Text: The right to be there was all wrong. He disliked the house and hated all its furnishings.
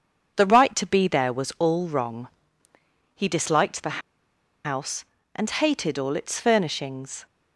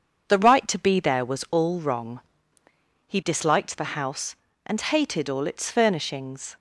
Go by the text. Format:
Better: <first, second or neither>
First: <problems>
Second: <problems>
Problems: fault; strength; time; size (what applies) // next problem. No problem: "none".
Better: second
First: pauses between "the" and "house"; noticeable; at 3.9 s; 0.64 s long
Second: none